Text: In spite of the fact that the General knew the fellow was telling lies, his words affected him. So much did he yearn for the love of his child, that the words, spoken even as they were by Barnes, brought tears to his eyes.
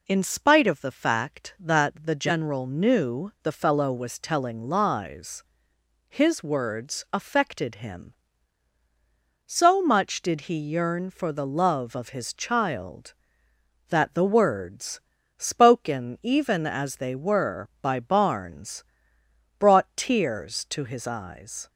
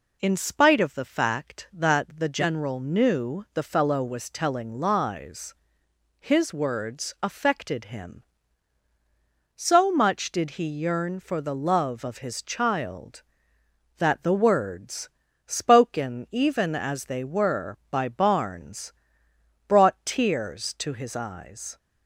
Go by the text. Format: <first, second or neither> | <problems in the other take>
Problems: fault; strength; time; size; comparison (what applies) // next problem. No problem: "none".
neither | none